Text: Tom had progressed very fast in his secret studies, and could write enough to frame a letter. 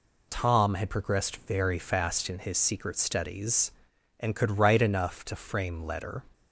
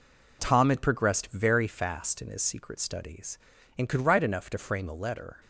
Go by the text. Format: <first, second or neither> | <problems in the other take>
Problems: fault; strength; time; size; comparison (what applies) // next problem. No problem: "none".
second | skips "a"; at 5.8 s